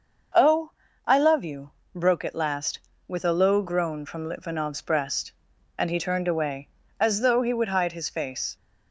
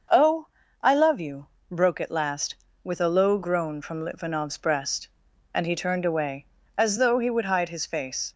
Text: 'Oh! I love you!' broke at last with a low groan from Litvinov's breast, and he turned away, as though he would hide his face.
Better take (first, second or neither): neither